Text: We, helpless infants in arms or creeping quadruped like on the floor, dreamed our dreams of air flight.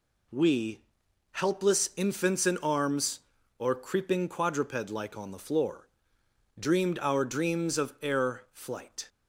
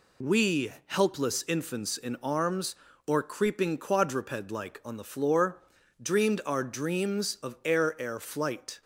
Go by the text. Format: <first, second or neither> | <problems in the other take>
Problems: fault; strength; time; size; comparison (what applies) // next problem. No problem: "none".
first | says "air" twice; at 7.9 s